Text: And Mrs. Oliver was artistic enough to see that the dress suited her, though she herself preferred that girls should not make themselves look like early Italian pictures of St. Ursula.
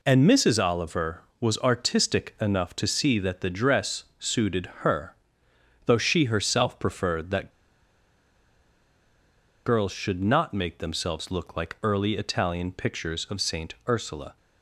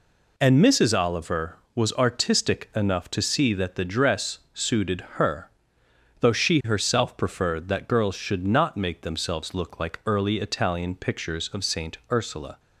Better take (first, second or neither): second